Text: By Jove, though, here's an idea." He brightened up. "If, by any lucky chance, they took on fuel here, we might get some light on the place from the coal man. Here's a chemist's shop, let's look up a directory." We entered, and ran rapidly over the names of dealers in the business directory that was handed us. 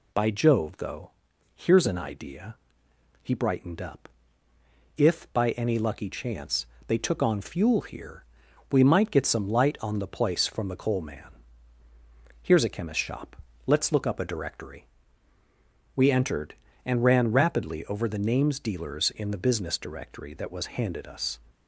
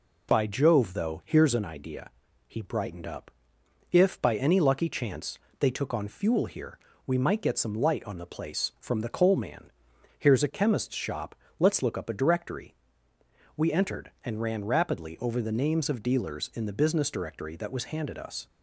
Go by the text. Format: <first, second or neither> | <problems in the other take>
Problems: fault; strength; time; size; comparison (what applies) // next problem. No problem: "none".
second | skips "of"; at 18.5 s